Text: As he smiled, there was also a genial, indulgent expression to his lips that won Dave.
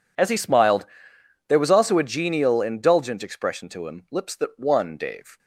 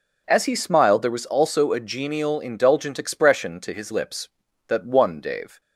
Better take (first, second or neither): second